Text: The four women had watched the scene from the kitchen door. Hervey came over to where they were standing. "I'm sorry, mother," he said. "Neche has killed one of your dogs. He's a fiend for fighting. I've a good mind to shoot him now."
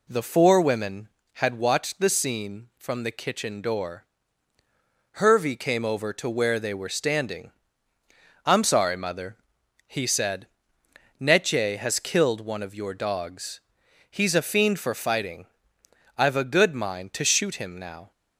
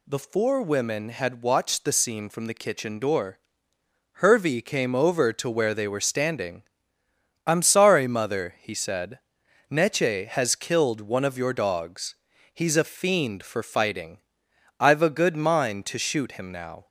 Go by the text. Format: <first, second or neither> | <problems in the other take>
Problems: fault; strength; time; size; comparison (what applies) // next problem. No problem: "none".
neither | none